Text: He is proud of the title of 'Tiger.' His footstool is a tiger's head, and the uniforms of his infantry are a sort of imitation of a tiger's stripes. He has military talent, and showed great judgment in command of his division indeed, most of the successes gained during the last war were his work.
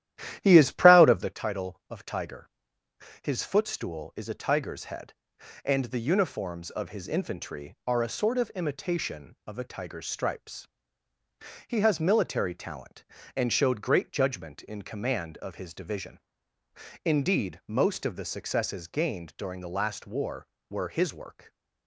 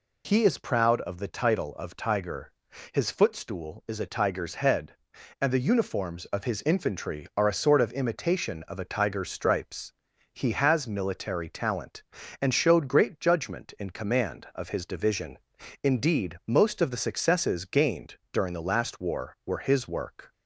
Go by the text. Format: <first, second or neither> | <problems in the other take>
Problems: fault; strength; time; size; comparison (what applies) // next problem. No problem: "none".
second | starts louder than the rest; strong; until 1.4 s; 12.5 dB // pauses between "division" and "indeed"; noticeable; at 16.2 s; 0.82 s long; noticeable in the second